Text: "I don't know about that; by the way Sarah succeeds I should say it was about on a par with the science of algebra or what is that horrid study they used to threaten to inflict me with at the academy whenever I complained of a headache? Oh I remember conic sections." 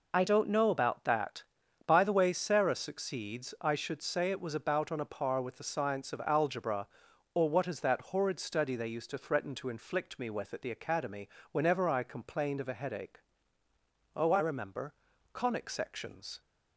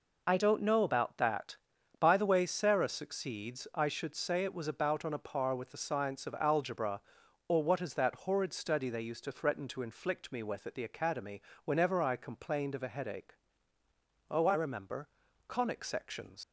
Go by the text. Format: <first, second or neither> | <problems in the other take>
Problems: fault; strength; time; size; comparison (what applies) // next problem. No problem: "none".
first | pauses between "academy" and "whenever"; slight; at 11.4 s; 0.24 s long; slight in the first // pauses between "remember" and "conic"; at 15.0 s; 0.38 s long; also in the first // leaves "sections" unfinished; at 16.4 s; 110 ms